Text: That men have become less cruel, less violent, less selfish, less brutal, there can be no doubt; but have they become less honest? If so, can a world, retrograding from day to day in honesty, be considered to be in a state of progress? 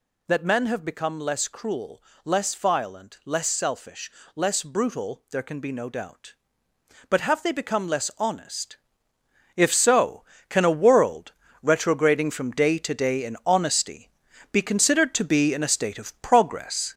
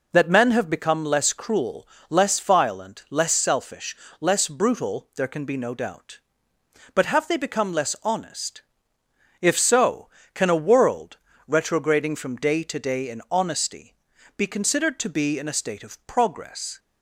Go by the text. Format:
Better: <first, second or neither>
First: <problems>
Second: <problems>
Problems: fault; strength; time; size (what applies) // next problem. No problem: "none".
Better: second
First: gets louder; noticeable; throughout; 5.5 dB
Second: none